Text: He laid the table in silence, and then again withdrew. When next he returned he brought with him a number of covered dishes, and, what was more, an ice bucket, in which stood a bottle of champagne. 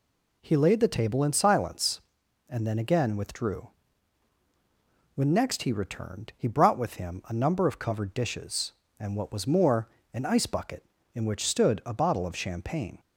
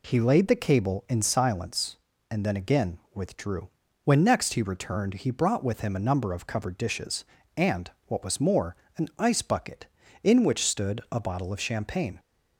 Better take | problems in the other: first | says "cable" for "table"; at 0.6 s // pauses between "again" and "withdrew"; slight; at 2.9 s; 0.16 s long

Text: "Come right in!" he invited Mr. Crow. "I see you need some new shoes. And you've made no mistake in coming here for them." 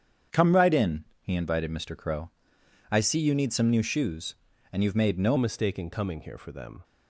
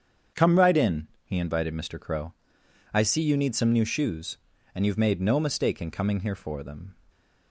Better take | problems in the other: second | starts louder than the rest; strong; until 1.4 s; 8 dB; strong in the second // changes voice at "mistake"; from 5.3 s on; 1.5 s long

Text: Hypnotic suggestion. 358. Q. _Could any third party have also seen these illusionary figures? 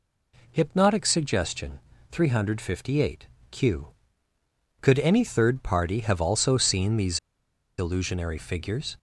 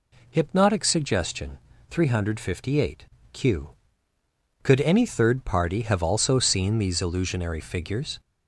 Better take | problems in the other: second | pauses between "these" and "illusionary"; noticeable; at 7.1 s; 0.60 s long

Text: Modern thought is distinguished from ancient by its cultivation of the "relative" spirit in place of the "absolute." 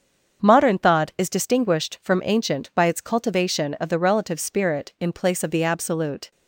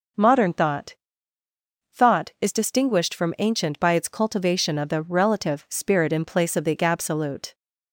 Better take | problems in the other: first | starts louder than the rest; noticeable; until 2.1 s; 6 dB; also in the first // says "thought" twice; at 1.9 s

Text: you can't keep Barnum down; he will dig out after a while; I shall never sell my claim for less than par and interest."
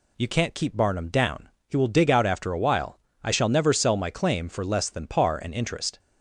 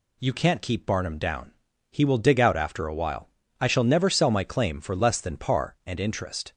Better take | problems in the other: neither | none

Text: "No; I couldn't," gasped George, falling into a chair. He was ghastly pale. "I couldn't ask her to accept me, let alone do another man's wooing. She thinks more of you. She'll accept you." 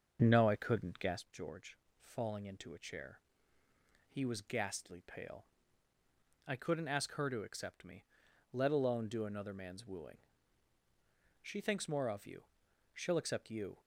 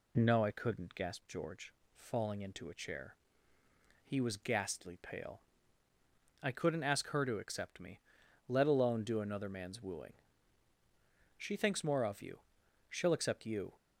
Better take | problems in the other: second | starts louder than the rest; until 1.2 s; 6.5 dB

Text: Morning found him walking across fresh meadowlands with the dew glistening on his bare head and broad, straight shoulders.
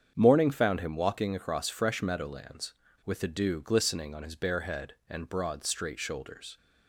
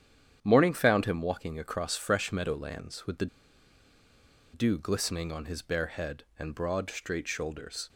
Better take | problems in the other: first | starts louder than the rest; strong; until 1.4 s; 9 dB; strong in the first // pauses between "the" and "dew"; strong; at 3.2 s; 1.2 s long

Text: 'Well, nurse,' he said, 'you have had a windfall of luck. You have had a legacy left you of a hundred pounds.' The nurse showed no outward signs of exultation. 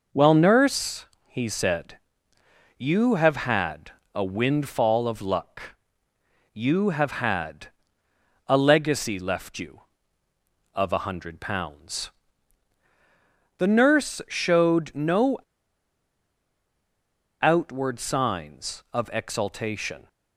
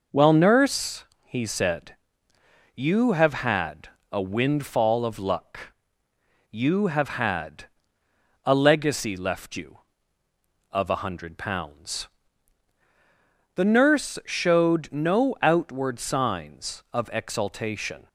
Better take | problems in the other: second | pauses between "had" and "a"; slight; at 3.9 s; 0.22 s long; slight in the second // pauses between "had" and "a"; noticeable; at 7.6 s; 0.78 s long; noticeable in the second // pauses between "no" and "outward"; strong; at 15.3 s; 2.0 s long

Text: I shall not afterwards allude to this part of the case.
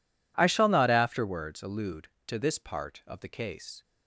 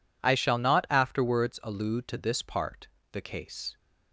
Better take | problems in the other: first | skips "of"; at 3.0 s

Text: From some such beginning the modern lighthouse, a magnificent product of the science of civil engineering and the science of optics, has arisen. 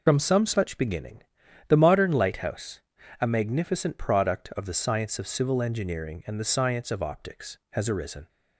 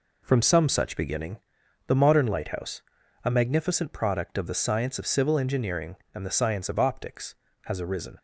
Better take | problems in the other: second | loses the start of "From"; at 0.0 s; 35 ms // pauses between "beginning" and "the"; noticeable; at 1.2 s; 0.48 s long; noticeable in the second

